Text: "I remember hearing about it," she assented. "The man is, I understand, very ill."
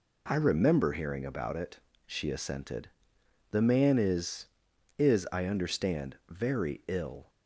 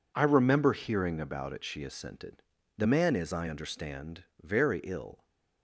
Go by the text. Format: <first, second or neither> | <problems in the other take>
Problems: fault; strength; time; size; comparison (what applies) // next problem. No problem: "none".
second | says "is" twice; at 4.9 s